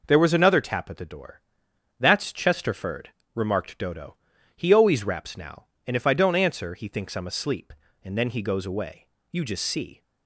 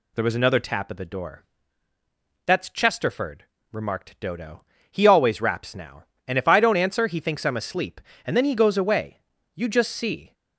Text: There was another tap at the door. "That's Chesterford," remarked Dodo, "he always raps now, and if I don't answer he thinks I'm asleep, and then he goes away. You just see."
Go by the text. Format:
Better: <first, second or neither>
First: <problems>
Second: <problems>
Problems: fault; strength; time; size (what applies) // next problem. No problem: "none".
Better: neither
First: none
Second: none